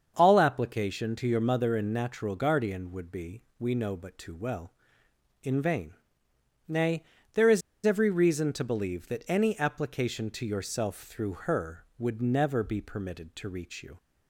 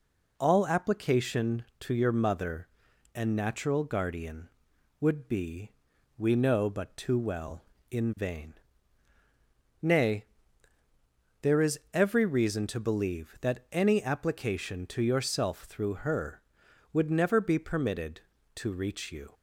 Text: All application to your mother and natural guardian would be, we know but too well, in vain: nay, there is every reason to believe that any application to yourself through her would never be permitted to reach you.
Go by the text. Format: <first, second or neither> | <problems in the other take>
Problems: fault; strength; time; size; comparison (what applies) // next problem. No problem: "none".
second | starts louder than the rest; until 1.1 s; 7 dB // pauses between "is" and "every"; slight; at 7.6 s; 0.25 s long // pauses between "through" and "her"; slight; at 11.3 s; 0.16 s long